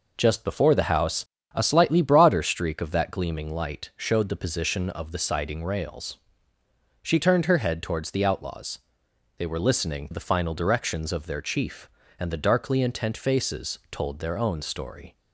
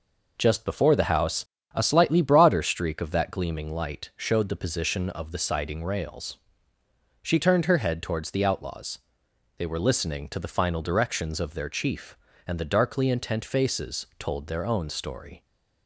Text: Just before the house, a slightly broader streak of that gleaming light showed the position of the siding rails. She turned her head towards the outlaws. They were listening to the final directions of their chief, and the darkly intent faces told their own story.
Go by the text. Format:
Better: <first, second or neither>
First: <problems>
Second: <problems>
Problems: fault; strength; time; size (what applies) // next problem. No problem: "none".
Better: second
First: skips "to"; at 10.0 s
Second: none